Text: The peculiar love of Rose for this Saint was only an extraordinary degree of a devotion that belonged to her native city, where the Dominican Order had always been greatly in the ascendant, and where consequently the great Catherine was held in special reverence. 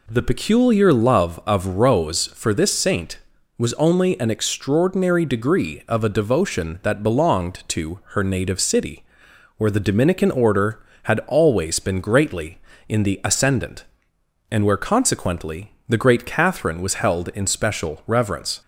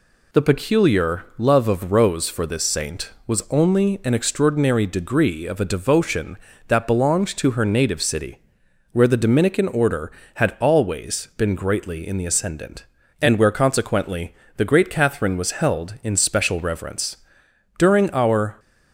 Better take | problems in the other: first | pauses between "consequently" and "the"; slight; at 14.3 s; 0.22 s long; slight in the first // goes on to say "During our"; noticeable; from 17.7 s on; 0.80 s long

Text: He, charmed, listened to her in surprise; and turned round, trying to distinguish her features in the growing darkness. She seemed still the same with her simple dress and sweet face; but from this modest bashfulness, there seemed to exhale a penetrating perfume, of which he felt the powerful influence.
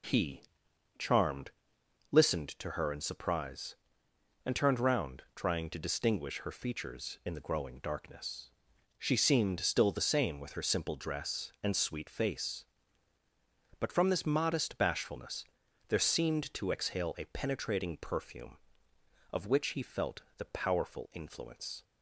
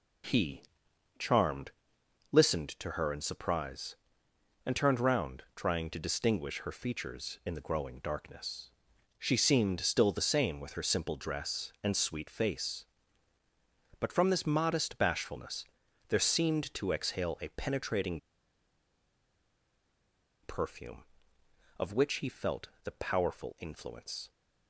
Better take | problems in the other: first | pauses between "penetrating" and "perfume"; strong; at 18.2 s; 2.2 s long

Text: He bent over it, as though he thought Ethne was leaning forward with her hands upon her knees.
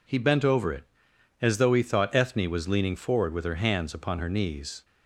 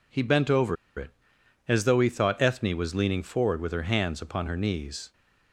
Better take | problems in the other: first | pauses between "over" and "it"; slight; at 0.7 s; 0.22 s long

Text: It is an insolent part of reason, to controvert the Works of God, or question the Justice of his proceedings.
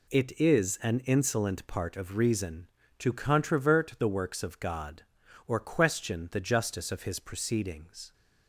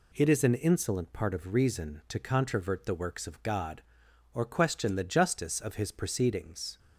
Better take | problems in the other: neither | none

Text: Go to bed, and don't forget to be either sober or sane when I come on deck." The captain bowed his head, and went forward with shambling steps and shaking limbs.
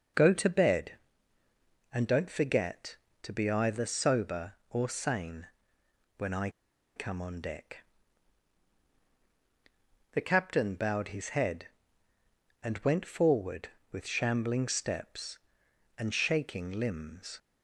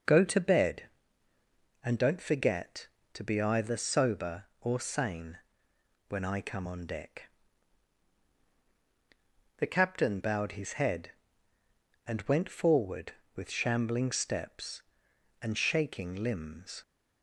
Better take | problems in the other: second | pauses between "sane" and "when"; noticeable; at 5.4 s; 0.70 s long; noticeable in the second // pauses between "I" and "come"; at 6.5 s; 0.45 s long

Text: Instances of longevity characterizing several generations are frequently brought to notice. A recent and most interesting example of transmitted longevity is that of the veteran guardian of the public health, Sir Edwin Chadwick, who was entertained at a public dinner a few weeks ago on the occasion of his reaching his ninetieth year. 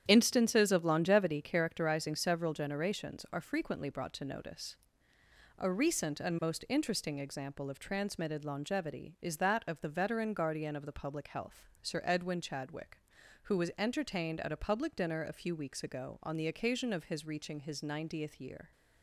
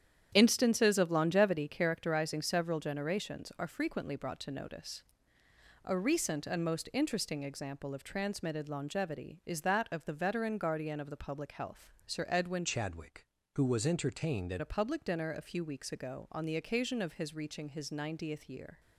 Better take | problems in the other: first | starts louder than the rest; strong; until 1.3 s; 9.5 dB; strong in the first // changes voice from "Chadwick" to "at"; from 12.6 to 14.6 s; 2.0 s long

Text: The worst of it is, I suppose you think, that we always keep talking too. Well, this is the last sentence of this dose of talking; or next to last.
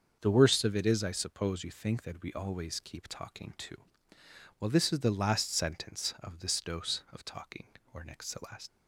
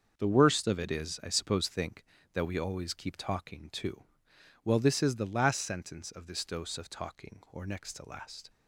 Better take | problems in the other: first | starts louder than the rest; until 1.1 s; 6.5 dB; also in the first // skips "you"; at 1.6 s

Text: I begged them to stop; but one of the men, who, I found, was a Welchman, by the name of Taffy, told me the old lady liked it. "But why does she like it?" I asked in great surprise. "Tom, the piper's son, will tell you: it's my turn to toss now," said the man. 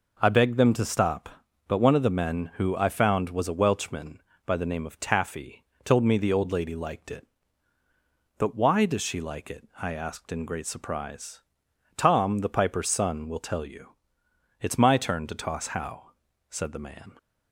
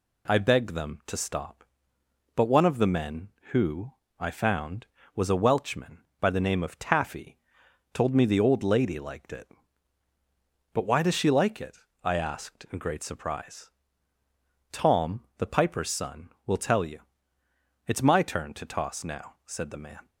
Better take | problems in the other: second | says "how" for "now"; at 15.6 s

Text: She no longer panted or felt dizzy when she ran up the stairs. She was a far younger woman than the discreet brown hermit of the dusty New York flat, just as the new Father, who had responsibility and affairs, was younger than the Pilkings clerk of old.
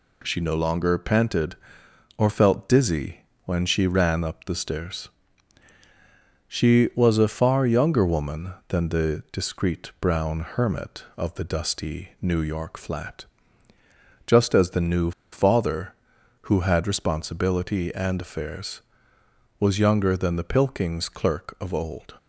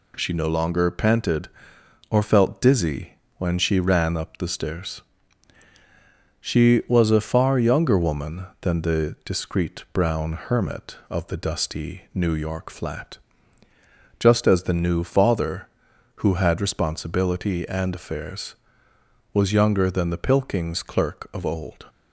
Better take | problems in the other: second | pauses between "dizzy" and "when"; slight; at 3.2 s; 0.22 s long; slight in the second // pauses between "new" and "Father"; slight; at 15.1 s; 0.21 s long

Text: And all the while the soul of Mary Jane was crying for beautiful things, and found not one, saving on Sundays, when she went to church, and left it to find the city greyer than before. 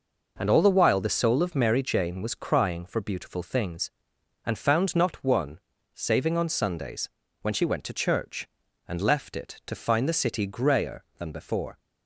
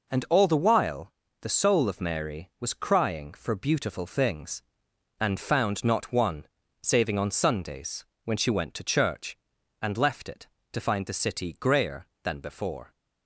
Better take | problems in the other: first | pauses between "while" and "the"; slight; at 1.1 s; 0.30 s long // skips "Jane"; at 2.5 s

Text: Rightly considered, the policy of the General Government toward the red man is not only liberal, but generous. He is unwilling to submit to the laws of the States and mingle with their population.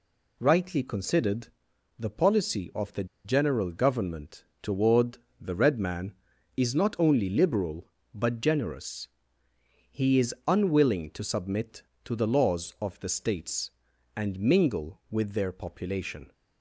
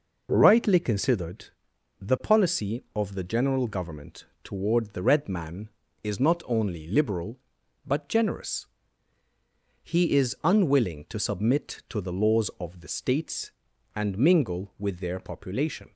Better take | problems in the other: second | pauses between "the" and "General"; slight; at 3.0 s; 0.19 s long // pauses between "Government" and "toward"; slight; at 4.4 s; 0.16 s long; slight in the second // pauses between "toward" and "the"; slight; at 5.1 s; 0.24 s long

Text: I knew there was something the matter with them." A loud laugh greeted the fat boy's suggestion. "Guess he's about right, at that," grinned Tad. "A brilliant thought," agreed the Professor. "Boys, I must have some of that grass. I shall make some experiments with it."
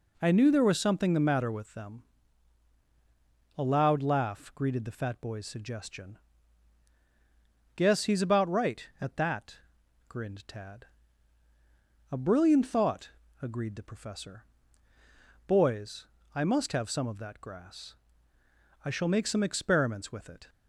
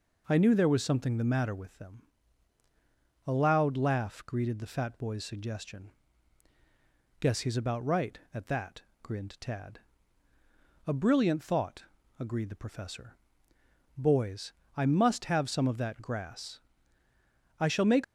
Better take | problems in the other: first | stops before "some experiments with it"; at 18.0 s

